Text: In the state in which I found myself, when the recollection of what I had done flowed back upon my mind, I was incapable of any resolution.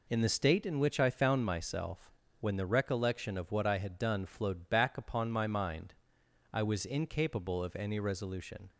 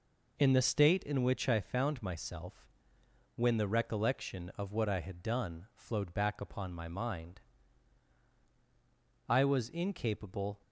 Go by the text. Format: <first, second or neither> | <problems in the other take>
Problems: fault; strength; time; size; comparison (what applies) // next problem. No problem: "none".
first | stops before "of any resolution"; at 10.6 s